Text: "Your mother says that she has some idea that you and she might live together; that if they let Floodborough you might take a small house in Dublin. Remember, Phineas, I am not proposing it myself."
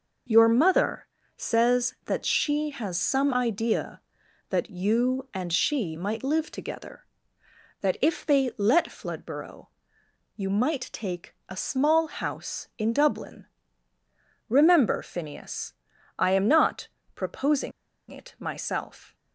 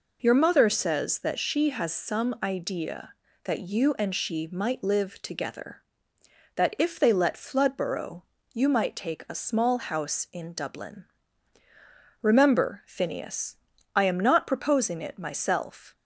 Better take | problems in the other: second | pauses between "mother" and "says"; slight; at 1.0 s; 0.30 s long // pauses between "Floodborough" and "you"; noticeable; at 9.6 s; 0.68 s long; slight in the second // pauses between "not" and "proposing"; slight; at 16.8 s; 0.26 s long // pauses between "proposing" and "it"; at 17.7 s; 0.38 s long

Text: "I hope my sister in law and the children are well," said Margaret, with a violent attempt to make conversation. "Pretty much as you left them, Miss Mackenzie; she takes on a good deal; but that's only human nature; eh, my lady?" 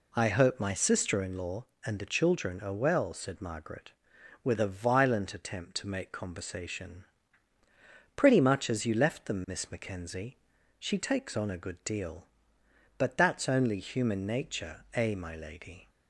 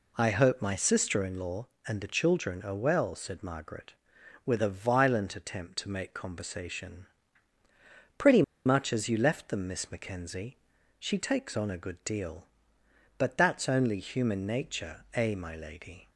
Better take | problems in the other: first | pauses between "Pretty" and "much"; slight; at 8.4 s; 0.23 s long

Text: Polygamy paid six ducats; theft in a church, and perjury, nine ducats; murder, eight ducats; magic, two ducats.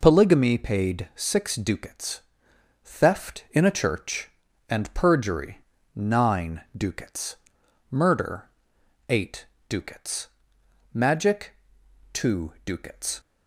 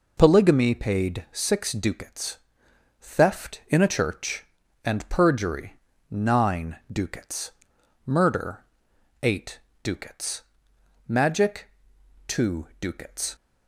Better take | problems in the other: neither | pauses between "eight" and "ducats"; slight; the same in both

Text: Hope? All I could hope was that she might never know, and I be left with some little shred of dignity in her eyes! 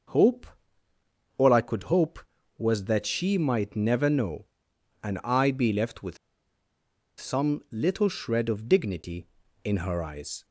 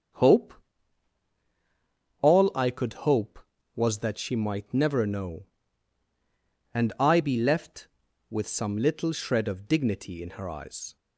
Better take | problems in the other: second | starts louder than the rest; until 2.0 s; 6 dB; also in the second // pauses between "with" and "some"; at 6.1 s; 1.0 s long

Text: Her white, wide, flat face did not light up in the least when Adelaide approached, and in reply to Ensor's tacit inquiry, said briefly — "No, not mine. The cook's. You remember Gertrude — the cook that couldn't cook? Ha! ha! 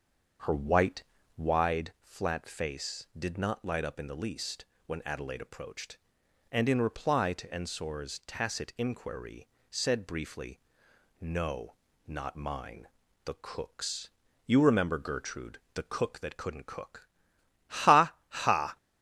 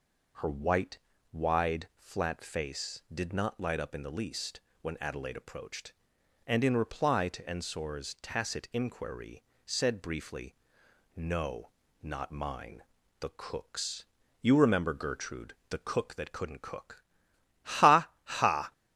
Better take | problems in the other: second | starts louder than the rest; until 1.7 s; 6.5 dB // pauses between "least" and "when"; slight; at 4.6 s; 0.22 s long; slight in the second

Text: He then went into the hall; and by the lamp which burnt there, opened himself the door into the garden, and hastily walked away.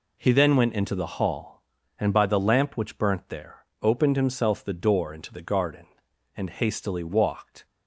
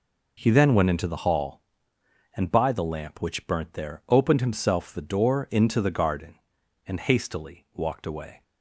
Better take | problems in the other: second | stops before "away"; at 7.6 s

